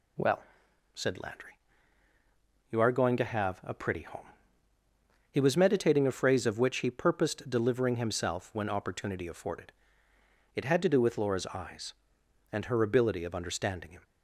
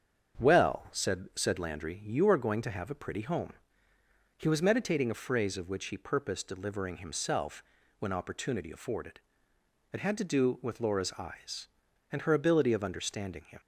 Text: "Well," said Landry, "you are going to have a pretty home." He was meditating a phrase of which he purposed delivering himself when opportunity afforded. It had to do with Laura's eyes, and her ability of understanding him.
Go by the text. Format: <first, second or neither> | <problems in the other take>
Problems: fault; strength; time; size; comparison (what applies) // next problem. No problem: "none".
first | starts louder than the rest; strong; until 1.4 s; 7.5 dB // says "said" twice; at 1.3 s // pauses between "himself" and "when"; slight; at 7.6 s; 0.36 s long